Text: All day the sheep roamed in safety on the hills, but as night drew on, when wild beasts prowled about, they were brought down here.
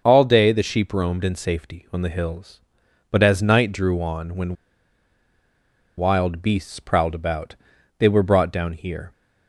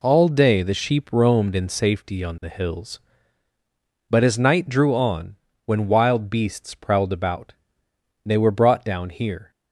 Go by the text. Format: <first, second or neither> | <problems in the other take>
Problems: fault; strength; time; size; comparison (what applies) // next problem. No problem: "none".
second | starts louder than the rest; until 1.0 s; 6.5 dB // pauses between "when" and "wild"; strong; at 4.5 s; 1.4 s long